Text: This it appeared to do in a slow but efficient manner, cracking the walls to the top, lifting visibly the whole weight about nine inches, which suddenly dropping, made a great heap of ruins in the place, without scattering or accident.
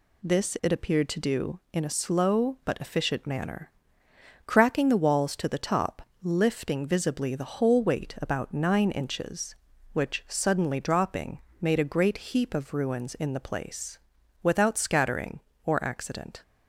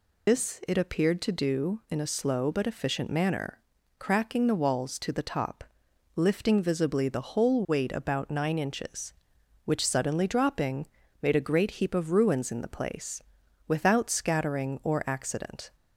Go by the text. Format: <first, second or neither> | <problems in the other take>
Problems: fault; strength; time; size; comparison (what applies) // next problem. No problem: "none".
first | loses the start of "This"; at 0.2 s; 105 ms